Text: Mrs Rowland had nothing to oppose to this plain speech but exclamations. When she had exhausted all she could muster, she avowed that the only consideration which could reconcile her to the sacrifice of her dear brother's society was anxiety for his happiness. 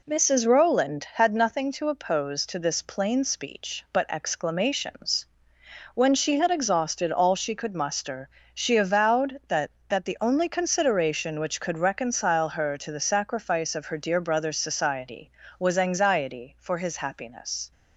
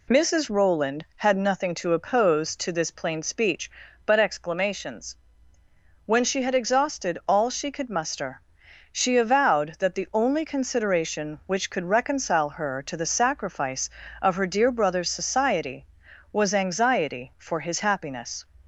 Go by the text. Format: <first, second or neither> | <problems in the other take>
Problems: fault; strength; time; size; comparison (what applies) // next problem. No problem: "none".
second | says "that" twice; at 9.8 s